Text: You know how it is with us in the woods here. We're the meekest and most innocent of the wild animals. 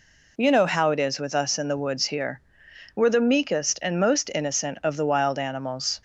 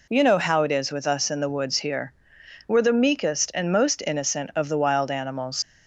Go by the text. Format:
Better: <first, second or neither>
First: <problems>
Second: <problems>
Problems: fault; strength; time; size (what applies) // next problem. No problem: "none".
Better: first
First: none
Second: leaves "animals" unfinished; at 5.6 s; 110 ms